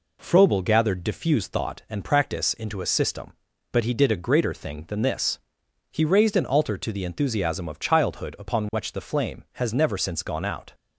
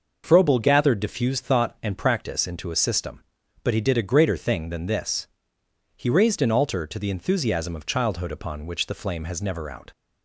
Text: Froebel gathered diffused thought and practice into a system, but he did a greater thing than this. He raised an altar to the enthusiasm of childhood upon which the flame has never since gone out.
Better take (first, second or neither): first